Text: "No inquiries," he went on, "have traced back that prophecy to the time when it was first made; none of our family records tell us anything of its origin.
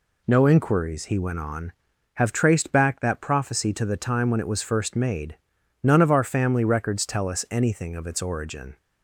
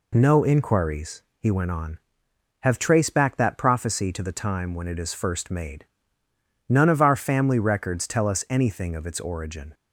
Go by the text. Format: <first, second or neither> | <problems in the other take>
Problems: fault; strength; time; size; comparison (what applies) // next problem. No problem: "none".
first | says "is" for "was"; at 4.9 s